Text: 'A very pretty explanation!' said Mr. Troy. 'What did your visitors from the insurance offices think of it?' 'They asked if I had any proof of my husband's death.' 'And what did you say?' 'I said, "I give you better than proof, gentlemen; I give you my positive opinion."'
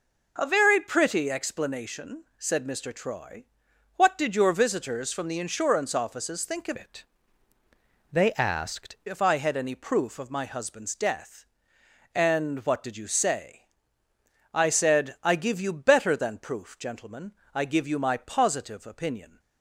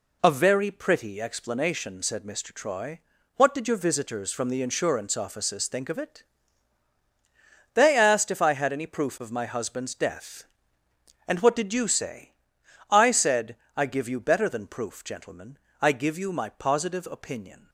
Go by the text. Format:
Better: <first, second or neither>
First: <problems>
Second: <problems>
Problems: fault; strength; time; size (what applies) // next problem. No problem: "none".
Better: second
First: changes voice from "it" to "asked"; from 6.7 to 8.9 s; 2.2 s long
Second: none